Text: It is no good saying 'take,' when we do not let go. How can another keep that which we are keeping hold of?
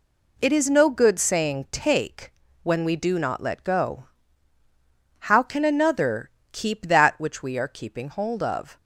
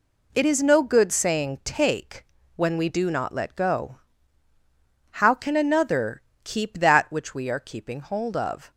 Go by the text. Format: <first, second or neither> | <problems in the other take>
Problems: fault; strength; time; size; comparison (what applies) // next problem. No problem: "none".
neither | pauses between "another" and "keep"; slight; the same in both